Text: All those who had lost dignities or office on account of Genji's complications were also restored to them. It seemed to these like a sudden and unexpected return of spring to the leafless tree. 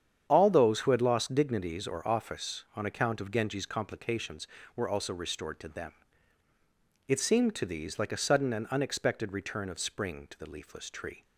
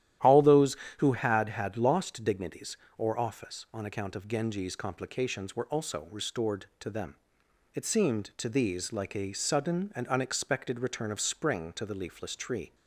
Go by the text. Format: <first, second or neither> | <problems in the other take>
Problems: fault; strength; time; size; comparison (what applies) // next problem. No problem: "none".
first | starts louder than the rest; strong; until 1.4 s; 12 dB; strong in the first // says "had" twice; at 1.4 s